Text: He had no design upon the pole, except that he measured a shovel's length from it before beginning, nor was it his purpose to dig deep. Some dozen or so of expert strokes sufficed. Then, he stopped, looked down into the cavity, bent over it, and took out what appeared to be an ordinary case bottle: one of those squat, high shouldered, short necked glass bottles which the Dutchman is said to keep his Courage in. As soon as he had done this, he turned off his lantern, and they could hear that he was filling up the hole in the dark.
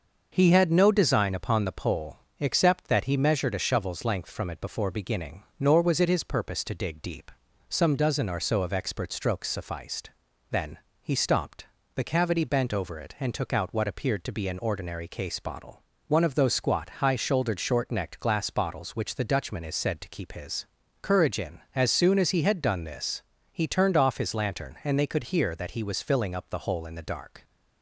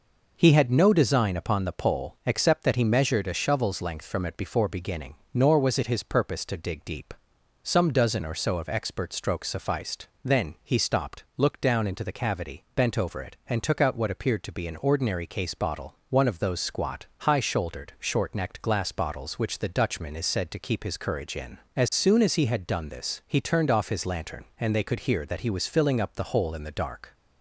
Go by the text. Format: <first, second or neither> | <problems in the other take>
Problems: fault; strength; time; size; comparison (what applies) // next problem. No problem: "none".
second | starts louder than the rest; until 1.3 s; 6 dB // skips "looked down into"; at 11.8 s // pauses between "his" and "Courage"; slight; at 20.6 s; 0.36 s long